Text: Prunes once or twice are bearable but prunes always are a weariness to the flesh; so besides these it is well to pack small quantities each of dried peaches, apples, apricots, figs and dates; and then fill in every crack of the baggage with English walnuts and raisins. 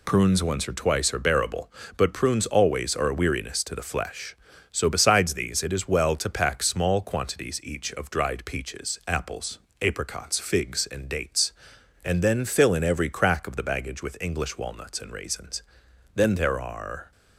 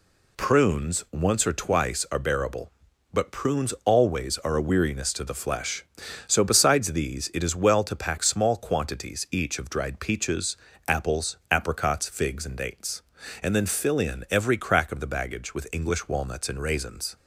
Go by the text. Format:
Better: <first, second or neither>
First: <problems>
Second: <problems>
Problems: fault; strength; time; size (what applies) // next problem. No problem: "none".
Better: second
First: goes on to say "Then there are"; noticeable; from 16.1 s on; 0.98 s long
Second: none